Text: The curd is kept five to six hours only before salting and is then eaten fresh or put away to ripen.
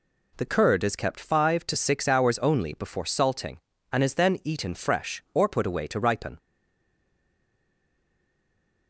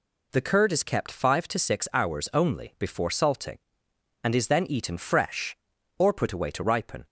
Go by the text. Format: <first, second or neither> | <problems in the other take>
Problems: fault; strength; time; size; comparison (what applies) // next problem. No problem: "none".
second | stays silent after the last word; from 6.3 s on; 2.5 s long